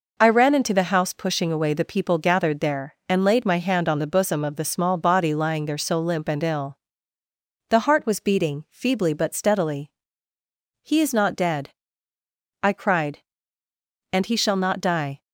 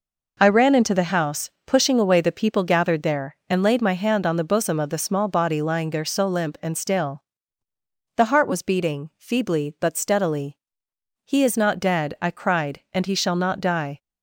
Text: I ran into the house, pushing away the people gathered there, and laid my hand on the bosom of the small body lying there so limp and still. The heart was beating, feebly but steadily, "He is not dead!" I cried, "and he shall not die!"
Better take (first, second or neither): second